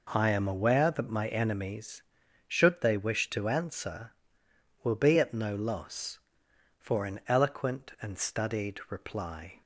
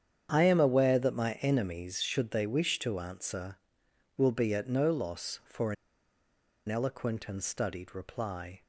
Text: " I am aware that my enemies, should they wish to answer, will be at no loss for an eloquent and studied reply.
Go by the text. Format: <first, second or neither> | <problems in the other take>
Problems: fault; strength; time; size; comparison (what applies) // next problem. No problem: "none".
first | starts louder than the rest; strong; until 1.3 s; 8.5 dB // pauses between "for" and "an"; noticeable; at 5.7 s; 0.94 s long